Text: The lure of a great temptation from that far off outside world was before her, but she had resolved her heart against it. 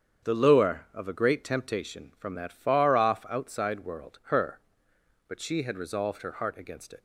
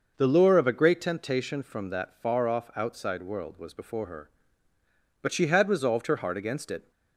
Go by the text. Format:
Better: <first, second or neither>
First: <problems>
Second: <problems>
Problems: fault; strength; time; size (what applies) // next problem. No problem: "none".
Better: second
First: starts louder than the rest; strong; until 1.3 s; 8 dB // skips "was before"; at 4.2 s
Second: none